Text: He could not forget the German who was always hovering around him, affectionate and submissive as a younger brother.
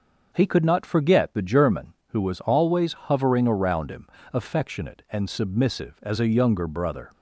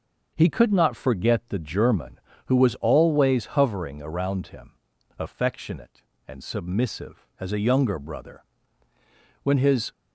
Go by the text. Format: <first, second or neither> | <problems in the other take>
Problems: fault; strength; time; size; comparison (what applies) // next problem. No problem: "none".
first | starts louder than the rest; until 1.3 s; 6.5 dB; also in the first // goes on to say "When his"; slight; from 9.4 s on; 0.48 s long